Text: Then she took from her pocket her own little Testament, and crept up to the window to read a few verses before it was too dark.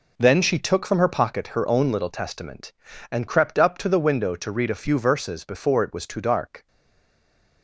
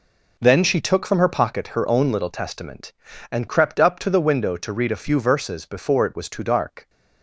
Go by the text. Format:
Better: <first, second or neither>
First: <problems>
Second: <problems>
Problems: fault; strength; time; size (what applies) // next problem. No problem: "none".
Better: second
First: stays silent after the last word; from 6.6 s on; 1.0 s long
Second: none